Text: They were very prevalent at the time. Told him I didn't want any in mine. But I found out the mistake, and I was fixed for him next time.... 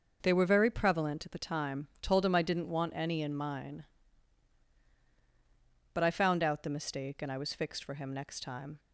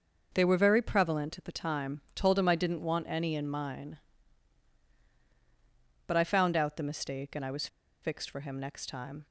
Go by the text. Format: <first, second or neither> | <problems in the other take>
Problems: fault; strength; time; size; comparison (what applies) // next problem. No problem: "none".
first | pauses between "was" and "fixed"; slight; at 7.6 s; 0.35 s long